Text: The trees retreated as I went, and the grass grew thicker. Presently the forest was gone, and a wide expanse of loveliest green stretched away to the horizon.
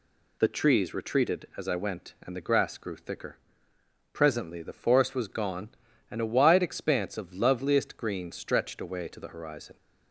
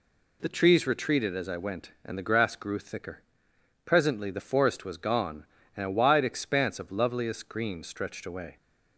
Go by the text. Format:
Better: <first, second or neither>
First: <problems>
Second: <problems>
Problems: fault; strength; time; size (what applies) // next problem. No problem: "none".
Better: first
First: none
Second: stops before "to the horizon"; at 8.5 s